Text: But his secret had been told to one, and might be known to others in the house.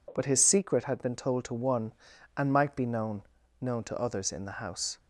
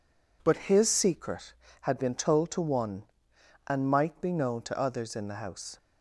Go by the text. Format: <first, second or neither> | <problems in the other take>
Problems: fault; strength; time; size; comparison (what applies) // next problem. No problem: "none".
second | says "known" twice; at 3.6 s